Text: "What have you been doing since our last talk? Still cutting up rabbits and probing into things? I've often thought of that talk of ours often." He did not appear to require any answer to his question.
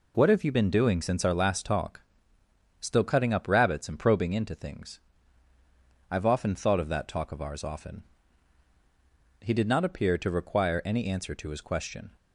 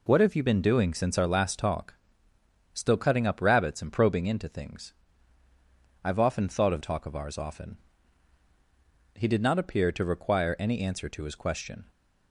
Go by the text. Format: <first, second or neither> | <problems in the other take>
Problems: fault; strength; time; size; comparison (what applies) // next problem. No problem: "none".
first | skips "that"; at 6.8 s